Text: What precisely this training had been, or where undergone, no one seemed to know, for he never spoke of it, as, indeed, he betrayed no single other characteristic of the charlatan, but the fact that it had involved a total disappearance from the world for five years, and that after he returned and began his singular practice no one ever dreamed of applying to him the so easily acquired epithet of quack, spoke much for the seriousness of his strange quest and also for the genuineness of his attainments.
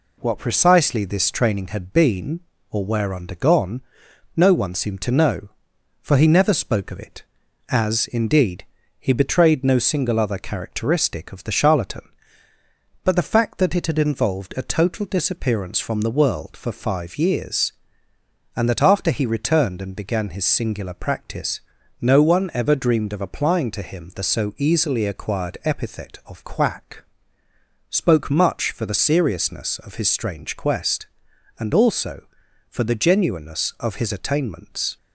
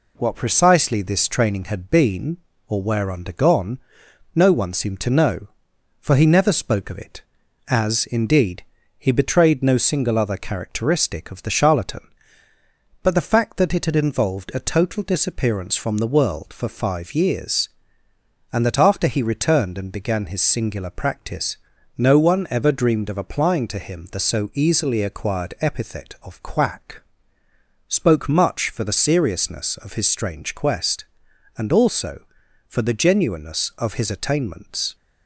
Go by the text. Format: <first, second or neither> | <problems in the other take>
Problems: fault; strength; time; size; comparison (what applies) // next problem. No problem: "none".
neither | pauses between "practice" and "no"; the same in both